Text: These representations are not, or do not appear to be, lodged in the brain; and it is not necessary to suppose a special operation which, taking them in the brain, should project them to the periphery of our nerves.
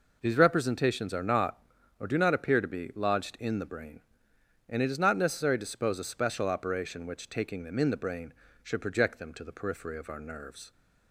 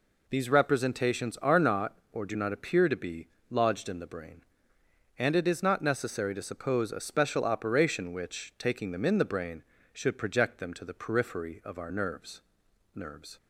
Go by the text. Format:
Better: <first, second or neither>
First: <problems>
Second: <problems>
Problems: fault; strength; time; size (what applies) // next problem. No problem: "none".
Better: first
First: none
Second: says "nerves" twice; at 12.9 s